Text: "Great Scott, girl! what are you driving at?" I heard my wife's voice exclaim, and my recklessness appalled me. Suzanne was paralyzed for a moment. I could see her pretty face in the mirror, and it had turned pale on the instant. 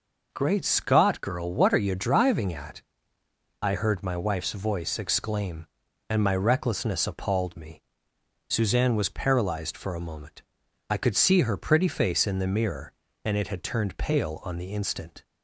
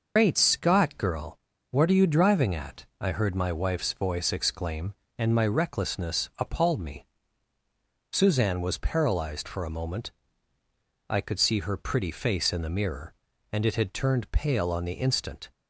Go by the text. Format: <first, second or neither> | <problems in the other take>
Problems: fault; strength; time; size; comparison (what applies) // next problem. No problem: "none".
first | loses the start of "Great"; at 0.1 s; 110 ms